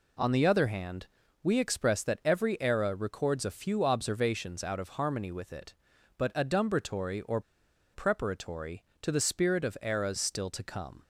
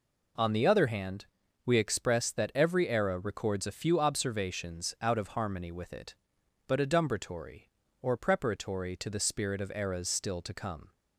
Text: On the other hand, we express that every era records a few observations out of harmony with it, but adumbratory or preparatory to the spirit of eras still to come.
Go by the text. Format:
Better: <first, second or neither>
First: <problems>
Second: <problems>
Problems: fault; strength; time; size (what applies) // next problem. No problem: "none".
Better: second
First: pauses between "or" and "preparatory"; noticeable; at 7.3 s; 0.53 s long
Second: none